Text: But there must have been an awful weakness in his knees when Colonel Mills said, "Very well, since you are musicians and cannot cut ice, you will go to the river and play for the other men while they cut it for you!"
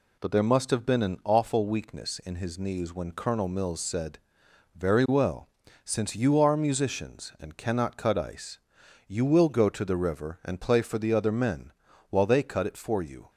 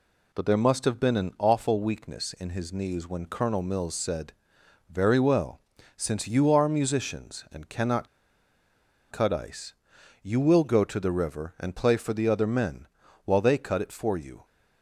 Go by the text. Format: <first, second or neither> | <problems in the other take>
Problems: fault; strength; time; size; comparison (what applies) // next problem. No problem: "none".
first | pauses between "cannot" and "cut"; at 8.0 s; 1.0 s long // pauses between "men" and "while"; at 12.8 s; 0.38 s long; also in the first